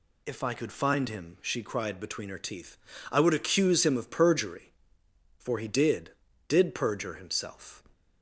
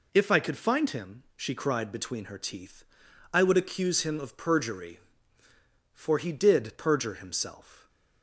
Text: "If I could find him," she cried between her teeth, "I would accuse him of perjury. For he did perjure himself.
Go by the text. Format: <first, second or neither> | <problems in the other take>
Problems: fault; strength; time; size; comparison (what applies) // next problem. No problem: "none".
second | says "did" twice; at 6.4 s